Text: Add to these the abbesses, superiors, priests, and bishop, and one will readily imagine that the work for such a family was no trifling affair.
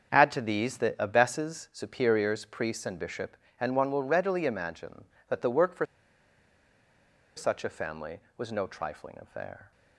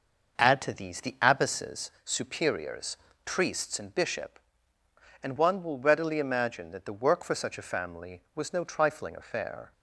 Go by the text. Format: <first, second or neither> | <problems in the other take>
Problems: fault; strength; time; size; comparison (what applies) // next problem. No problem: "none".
second | starts louder than the rest; strong; until 1.2 s; 8 dB; noticeable in the second // pauses between "for" and "such"; strong; at 5.8 s; 1.5 s long